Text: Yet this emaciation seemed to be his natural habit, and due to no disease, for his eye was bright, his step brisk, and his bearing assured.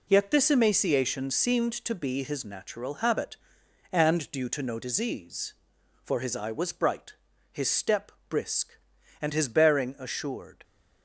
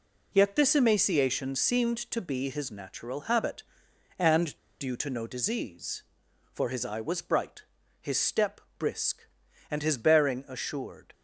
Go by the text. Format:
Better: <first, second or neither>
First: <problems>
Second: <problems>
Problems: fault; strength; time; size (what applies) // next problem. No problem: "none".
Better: first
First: pauses between "step" and "brisk"; slight; at 8.1 s; 0.18 s long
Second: pauses between "and" and "due"; slight; at 4.5 s; 0.22 s long // pauses between "step" and "brisk"; slight; at 8.6 s; 0.18 s long